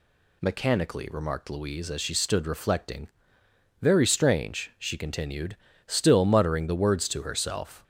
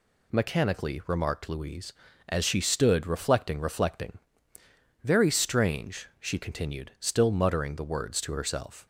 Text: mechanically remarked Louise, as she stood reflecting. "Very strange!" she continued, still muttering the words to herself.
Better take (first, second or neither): first